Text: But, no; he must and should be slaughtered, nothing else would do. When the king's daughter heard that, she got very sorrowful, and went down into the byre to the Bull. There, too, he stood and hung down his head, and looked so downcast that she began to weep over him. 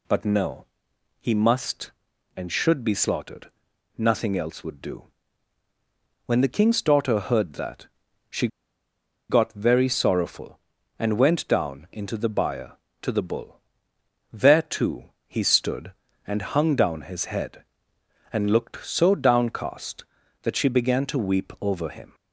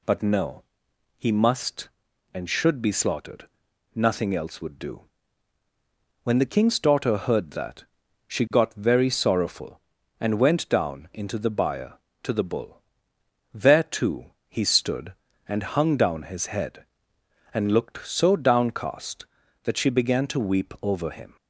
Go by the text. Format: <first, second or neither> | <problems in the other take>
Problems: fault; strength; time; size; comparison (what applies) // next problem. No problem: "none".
second | pauses between "she" and "got"; noticeable; at 8.4 s; 0.82 s long